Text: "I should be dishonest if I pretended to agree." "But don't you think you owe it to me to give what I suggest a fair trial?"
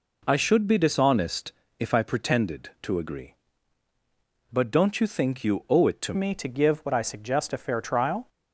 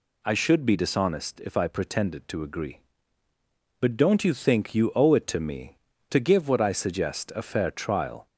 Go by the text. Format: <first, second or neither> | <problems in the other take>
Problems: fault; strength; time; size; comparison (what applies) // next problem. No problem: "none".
second | pauses between "dishonest" and "if"; slight; at 1.5 s; 0.26 s long // changes voice at "me"; from 6.1 s on; 2.1 s long